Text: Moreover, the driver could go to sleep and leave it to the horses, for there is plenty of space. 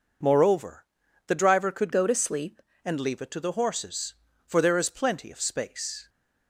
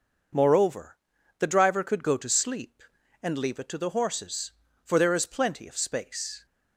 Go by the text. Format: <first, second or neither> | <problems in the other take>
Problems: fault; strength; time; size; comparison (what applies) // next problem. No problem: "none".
second | changes voice from "go" to "sleep"; from 1.9 to 2.6 s; 0.7 s long